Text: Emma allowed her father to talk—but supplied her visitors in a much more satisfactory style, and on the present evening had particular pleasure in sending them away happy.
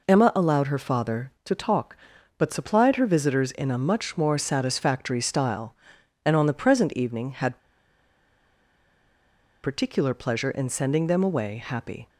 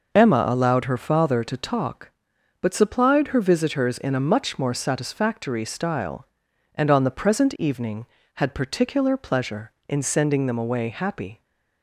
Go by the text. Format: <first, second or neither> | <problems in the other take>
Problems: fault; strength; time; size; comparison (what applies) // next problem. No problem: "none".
second | pauses between "had" and "particular"; strong; at 7.5 s; 2.0 s long